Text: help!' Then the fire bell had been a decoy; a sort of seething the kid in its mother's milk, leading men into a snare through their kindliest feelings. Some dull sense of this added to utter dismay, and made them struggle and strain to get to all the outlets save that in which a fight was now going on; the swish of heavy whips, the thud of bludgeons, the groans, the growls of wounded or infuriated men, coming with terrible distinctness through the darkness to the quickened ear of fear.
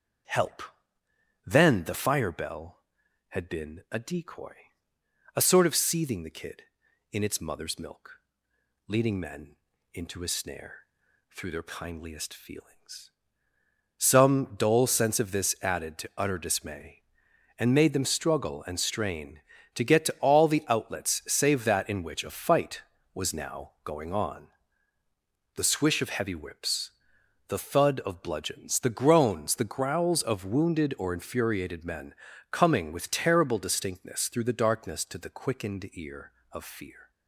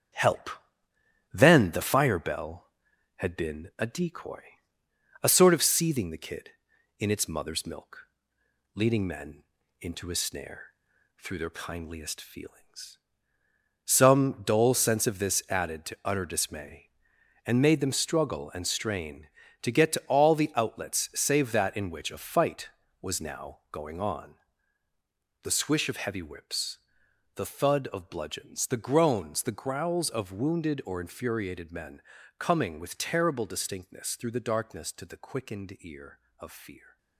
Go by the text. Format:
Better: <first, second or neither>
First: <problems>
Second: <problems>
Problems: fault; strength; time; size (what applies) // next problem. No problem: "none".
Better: first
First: starts louder than the rest; strong; until 2.1 s; 7.5 dB // pauses between "men" and "into"; at 9.5 s; 0.40 s long // pauses between "snare" and "through"; noticeable; at 10.7 s; 0.50 s long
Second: gets quieter; noticeable; throughout; 5 dB // starts louder than the rest; strong; until 2.0 s; 9 dB // pauses between "men" and "into"; at 9.4 s; 0.40 s long // pauses between "snare" and "through"; noticeable; at 10.6 s; 0.50 s long